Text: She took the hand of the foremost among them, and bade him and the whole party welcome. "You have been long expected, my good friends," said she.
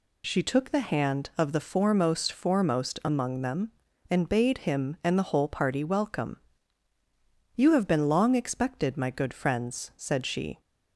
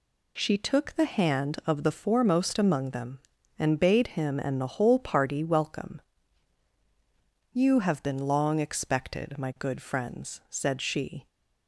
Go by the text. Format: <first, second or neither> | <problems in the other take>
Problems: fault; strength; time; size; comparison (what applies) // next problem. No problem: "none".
second | says "foremost" twice; at 2.3 s